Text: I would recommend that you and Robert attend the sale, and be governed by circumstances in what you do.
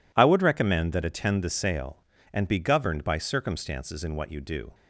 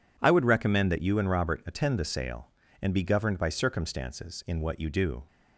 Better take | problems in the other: second | skips "you and Robert"; at 1.0 s

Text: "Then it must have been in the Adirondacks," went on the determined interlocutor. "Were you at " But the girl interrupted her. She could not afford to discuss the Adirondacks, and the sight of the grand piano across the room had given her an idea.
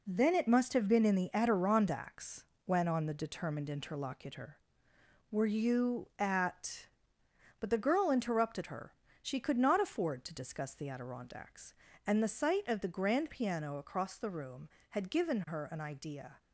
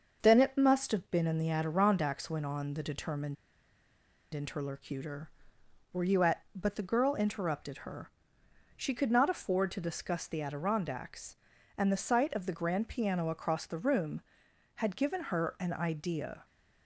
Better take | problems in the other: first | starts louder than the rest; until 1.2 s; 6.5 dB // pauses between "determined" and "interlocutor"; at 3.3 s; 0.99 s long

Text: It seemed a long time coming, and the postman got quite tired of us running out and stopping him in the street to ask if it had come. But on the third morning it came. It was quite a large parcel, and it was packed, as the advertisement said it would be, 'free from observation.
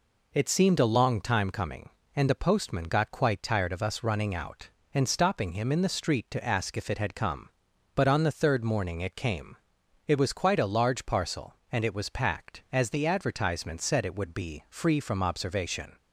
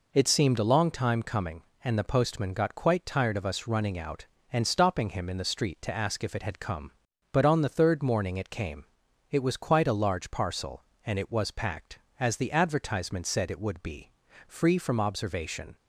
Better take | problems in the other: neither | none

